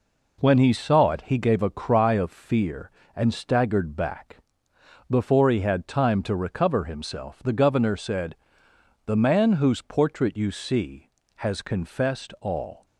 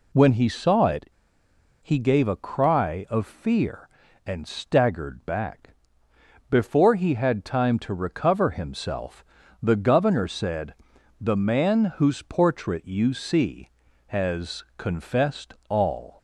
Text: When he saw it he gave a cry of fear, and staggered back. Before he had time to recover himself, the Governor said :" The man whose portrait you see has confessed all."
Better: first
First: none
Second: pauses between "it" and "he"; noticeable; at 1.0 s; 0.73 s long // pauses between "confessed" and "all"; slight; at 15.5 s; 0.16 s long

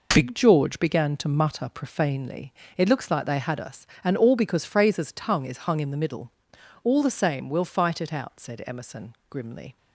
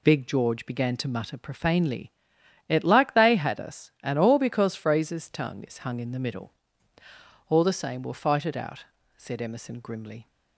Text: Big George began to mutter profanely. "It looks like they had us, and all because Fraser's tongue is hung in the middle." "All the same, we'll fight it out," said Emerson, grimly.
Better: first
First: none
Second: skips "looks"; at 2.8 s

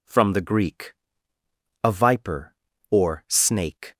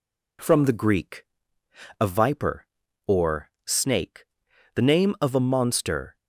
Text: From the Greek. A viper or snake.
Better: first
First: none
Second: pauses between "or" and "snake"; slight; at 3.4 s; 0.16 s long // goes on to say "The name of a monster"; from 4.7 s on; 1.4 s long

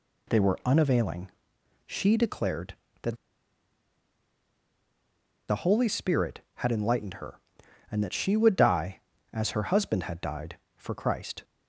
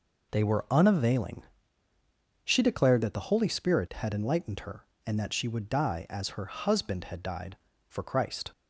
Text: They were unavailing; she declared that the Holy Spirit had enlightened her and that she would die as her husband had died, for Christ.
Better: second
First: pauses between "that" and "the"; strong; at 3.1 s; 2.3 s long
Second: none

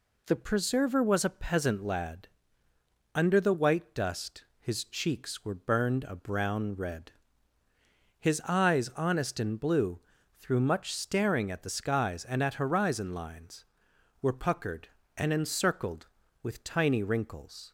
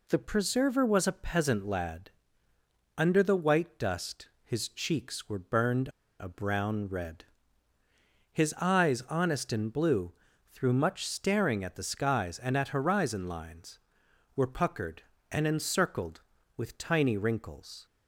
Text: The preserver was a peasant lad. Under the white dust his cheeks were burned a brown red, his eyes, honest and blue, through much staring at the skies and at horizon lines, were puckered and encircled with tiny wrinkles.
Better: first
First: none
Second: pauses between "burned" and "a"; slight; at 5.8 s; 0.31 s long

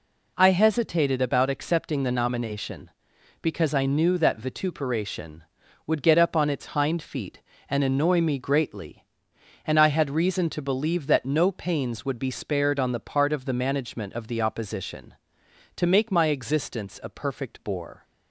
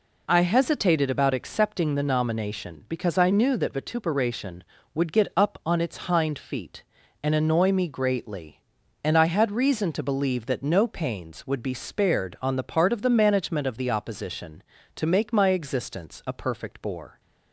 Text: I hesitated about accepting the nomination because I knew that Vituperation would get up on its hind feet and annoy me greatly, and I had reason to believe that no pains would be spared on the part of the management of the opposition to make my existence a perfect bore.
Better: neither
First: none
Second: none

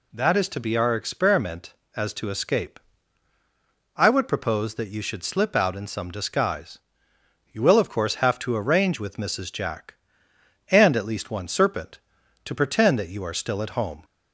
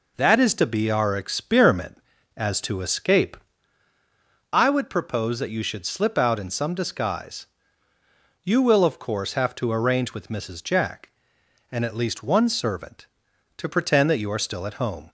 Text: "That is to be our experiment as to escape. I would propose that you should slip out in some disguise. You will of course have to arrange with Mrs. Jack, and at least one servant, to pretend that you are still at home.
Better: second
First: says "serpent" for "servant"; at 11.4 s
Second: none

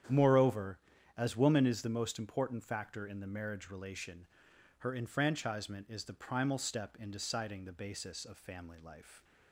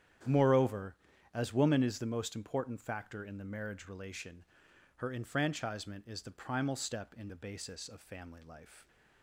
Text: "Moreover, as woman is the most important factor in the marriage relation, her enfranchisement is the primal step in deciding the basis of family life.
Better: first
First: starts louder than the rest; strong; until 1.4 s; 9 dB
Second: starts louder than the rest; strong; until 1.6 s; 9.5 dB // skips "deciding"; at 7.2 s

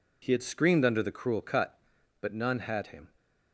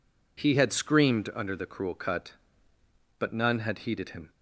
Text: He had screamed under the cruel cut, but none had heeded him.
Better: second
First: skips "heeded"; at 2.8 s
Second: none

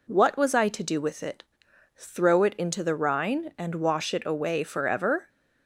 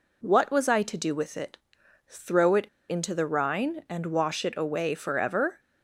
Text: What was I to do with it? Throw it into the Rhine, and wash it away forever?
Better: first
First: none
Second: pauses between "it" and "into"; slight; at 2.6 s; 0.22 s long

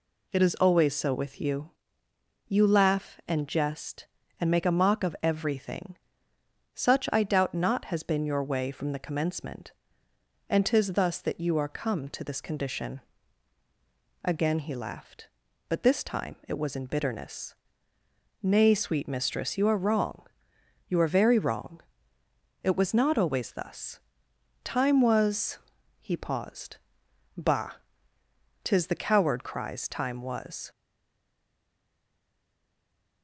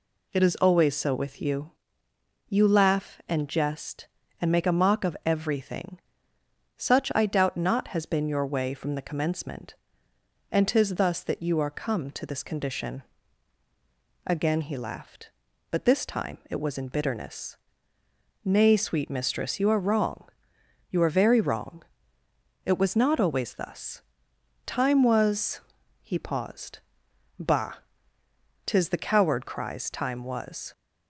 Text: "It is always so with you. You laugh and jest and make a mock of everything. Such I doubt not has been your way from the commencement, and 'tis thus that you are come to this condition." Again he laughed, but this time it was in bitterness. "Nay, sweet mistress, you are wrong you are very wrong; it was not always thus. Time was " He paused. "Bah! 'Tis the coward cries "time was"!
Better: second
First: pauses between "wrong" and "you"; noticeable; at 20.2 s; 0.62 s long // stays silent after the last word; from 30.6 s on; 2.6 s long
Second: pauses between "wrong" and "you"; noticeable; at 20.2 s; 0.62 s long

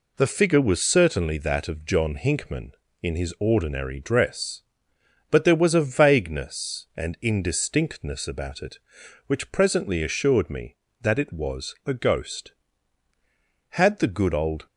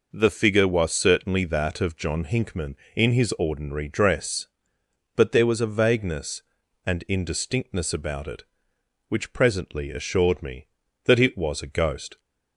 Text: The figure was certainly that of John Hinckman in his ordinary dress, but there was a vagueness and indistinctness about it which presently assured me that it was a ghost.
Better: second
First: goes on to say "Had the good old"; noticeable; from 13.7 s on; 0.92 s long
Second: none

